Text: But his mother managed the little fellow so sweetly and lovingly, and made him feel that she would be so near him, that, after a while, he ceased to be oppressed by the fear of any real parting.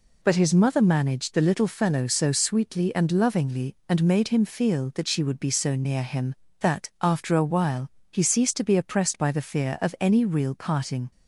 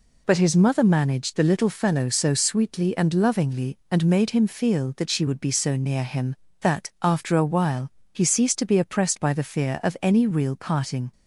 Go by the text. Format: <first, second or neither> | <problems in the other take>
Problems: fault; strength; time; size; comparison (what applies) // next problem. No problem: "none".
neither | none